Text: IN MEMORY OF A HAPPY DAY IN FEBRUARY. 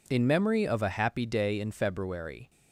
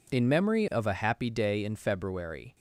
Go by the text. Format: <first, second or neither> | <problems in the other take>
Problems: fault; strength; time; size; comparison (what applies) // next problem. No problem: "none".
neither | none